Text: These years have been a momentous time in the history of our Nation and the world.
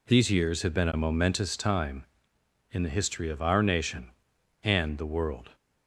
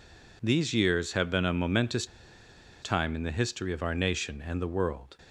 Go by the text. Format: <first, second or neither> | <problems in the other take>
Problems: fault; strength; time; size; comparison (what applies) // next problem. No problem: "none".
first | pauses between "momentous" and "time"; noticeable; at 2.0 s; 0.76 s long